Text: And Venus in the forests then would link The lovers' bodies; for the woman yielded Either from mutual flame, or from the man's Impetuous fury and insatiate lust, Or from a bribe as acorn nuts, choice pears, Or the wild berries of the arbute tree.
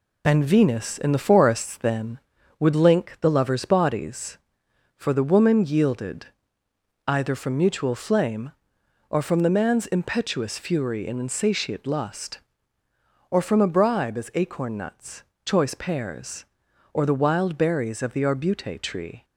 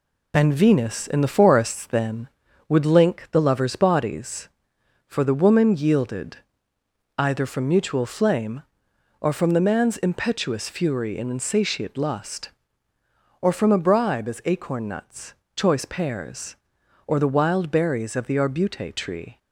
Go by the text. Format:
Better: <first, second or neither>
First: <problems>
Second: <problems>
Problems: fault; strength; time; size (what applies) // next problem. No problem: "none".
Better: neither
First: pauses between "yielded" and "Either"; noticeable; at 6.2 s; 0.78 s long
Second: pauses between "yielded" and "Either"; noticeable; at 6.3 s; 0.78 s long